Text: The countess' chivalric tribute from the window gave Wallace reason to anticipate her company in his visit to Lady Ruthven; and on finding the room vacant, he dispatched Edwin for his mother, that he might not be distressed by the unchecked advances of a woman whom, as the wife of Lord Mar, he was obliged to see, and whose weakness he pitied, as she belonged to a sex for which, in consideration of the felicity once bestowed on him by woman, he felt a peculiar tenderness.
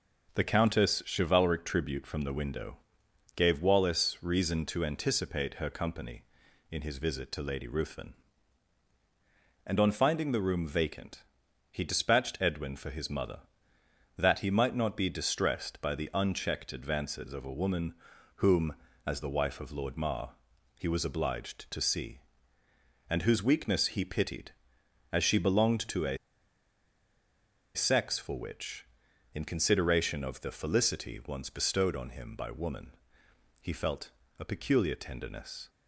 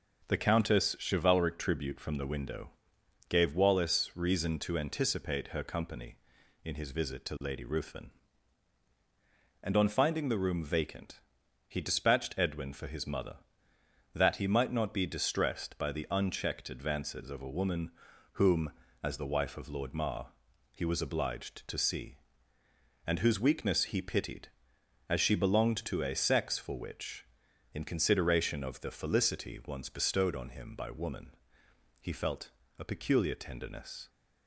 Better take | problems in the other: second | starts louder than the rest; until 1.5 s; 7 dB; also in the second // pauses between "window" and "gave"; noticeable; at 2.7 s; 0.58 s long; noticeable in the second // pauses between "woman" and "whom"; at 17.9 s; 0.42 s long; also in the second // pauses between "a" and "sex"; strong; at 26.1 s; 1.5 s long // pauses between "felt" and "a"; slight; at 34.0 s; 0.30 s long; slight in the second

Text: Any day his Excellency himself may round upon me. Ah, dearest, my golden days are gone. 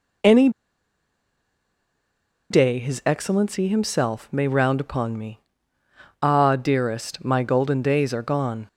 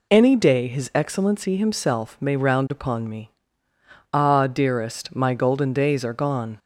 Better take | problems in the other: second | pauses between "Any" and "day"; strong; at 0.4 s; 2.0 s long

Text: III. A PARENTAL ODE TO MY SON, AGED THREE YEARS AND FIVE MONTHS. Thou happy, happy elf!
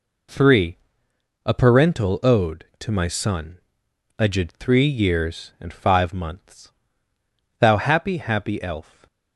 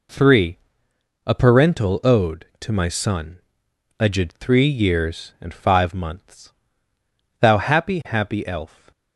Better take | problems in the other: neither | none

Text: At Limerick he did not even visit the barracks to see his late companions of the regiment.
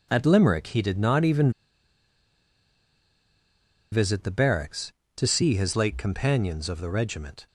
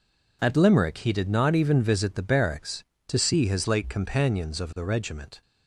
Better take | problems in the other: second | pauses between "even" and "visit"; strong; at 1.5 s; 2.4 s long

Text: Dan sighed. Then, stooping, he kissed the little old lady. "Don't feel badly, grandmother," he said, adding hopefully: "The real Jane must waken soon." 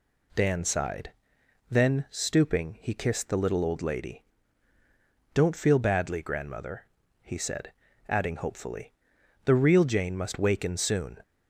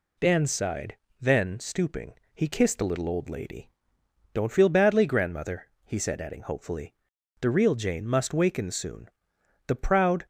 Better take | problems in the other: first | goes on to say "The proud"; from 9.6 s on; 0.58 s long

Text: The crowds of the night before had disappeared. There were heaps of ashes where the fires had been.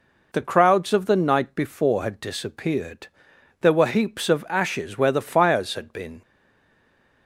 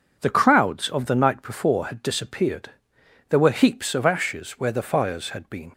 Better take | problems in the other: second | stays silent after the last word; from 6.2 s on; 1.0 s long

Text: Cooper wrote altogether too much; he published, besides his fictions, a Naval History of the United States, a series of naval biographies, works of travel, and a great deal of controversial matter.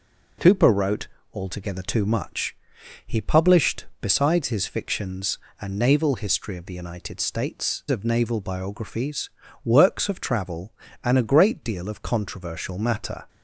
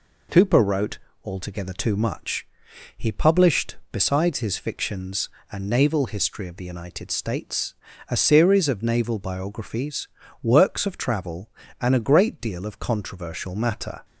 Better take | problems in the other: second | pauses between "wrote" and "altogether"; slight; at 1.0 s; 0.26 s long; slight in the second // skips "a series"; at 7.8 s

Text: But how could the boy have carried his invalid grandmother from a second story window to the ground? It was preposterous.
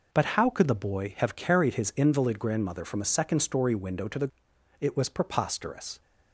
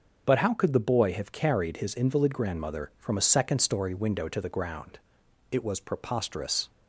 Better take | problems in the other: second | skips "ground"; at 4.5 s

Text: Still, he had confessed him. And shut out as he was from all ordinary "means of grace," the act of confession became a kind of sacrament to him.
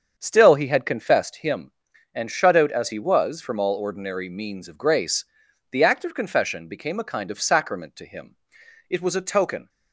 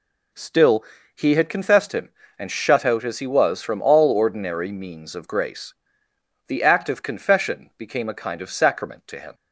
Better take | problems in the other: second | starts louder than the rest; strong; until 1.1 s; 7 dB // goes on to say "It was a token"; noticeable; from 8.8 s on; 0.80 s long

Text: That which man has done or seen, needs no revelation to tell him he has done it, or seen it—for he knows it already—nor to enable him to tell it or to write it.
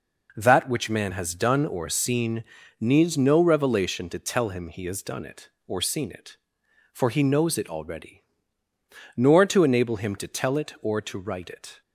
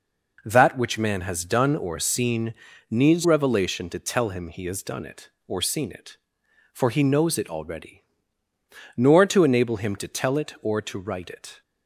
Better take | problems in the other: first | skips "no"; at 3.2 s

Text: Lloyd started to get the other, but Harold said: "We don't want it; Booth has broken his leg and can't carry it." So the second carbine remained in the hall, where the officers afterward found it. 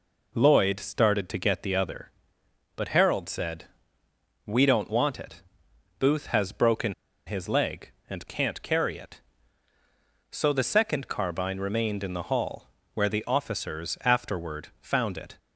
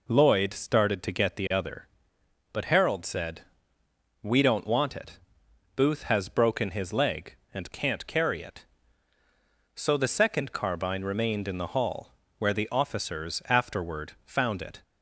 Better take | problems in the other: second | pauses between "broken" and "his"; slight; at 6.9 s; 0.33 s long

